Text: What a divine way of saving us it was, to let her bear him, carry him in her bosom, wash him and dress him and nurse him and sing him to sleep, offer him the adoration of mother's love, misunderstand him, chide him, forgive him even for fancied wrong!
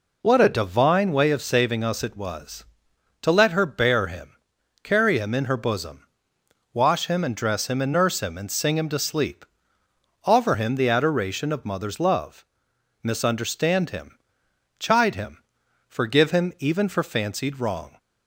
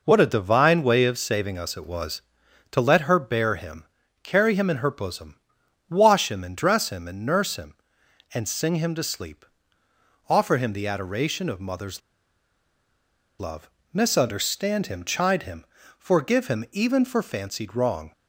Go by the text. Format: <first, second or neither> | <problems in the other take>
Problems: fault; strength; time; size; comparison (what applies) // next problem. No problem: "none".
first | pauses between "mother's" and "love"; strong; at 12.0 s; 1.3 s long